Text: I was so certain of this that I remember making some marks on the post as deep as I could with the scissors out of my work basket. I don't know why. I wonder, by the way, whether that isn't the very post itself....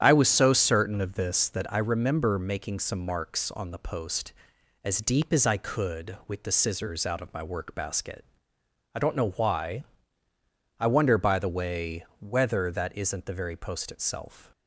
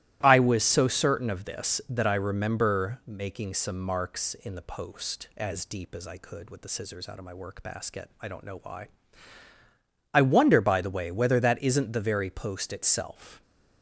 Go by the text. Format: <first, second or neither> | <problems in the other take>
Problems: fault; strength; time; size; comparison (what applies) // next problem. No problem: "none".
first | starts louder than the rest; strong; until 1.2 s; 15 dB; strong in the first // says "in" for "on"; at 4.3 s